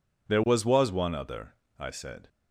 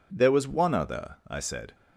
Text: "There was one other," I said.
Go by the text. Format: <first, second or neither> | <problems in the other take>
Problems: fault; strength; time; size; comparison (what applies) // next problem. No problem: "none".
second | says "was" twice; at 0.6 s